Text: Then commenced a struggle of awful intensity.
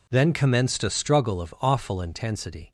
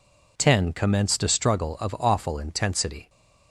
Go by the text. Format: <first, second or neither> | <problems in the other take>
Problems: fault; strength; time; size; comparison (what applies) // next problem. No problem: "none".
first | says "Ten" for "Then"; at 0.3 s